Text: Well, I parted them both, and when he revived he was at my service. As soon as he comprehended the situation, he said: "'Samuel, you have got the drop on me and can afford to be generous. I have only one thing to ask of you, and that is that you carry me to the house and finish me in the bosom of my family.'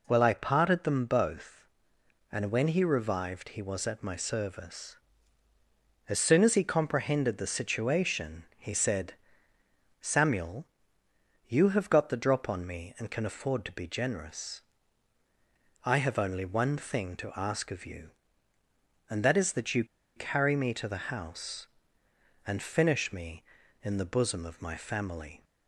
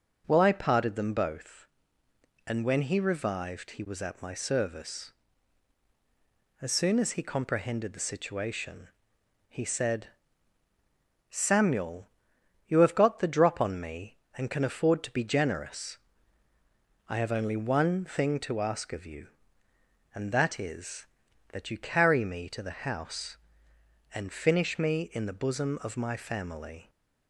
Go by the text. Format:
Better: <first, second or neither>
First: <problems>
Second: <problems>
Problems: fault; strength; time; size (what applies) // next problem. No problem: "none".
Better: second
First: pauses between "you" and "carry"; slight; at 19.8 s; 0.31 s long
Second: none